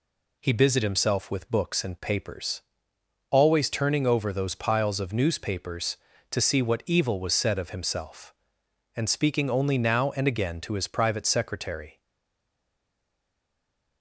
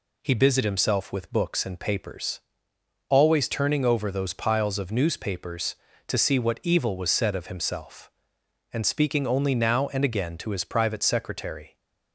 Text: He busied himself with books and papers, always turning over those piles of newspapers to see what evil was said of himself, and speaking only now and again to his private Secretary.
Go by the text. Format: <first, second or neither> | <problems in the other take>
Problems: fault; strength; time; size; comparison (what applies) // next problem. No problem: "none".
second | stays silent after the last word; noticeable; from 12.0 s on; 2.0 s long